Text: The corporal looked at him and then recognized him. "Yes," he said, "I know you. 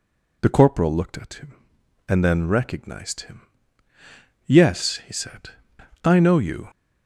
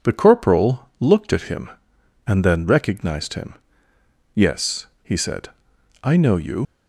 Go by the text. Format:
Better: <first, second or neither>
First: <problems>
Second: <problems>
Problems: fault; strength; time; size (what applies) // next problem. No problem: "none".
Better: first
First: none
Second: leaves "you" unfinished; at 6.6 s; 65 ms